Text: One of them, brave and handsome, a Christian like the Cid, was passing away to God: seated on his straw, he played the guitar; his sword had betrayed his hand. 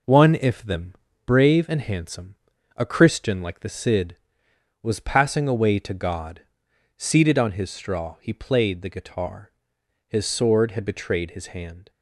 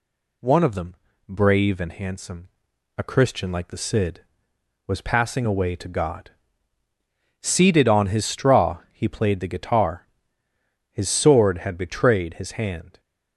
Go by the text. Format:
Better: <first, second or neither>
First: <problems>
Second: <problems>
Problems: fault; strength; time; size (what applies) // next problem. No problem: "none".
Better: second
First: says "if" for "of"; at 0.3 s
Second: none